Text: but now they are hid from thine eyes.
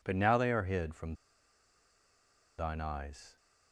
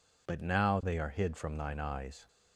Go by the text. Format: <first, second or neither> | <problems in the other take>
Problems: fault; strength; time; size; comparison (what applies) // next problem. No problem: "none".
second | pauses between "from" and "thine"; strong; at 1.1 s; 1.4 s long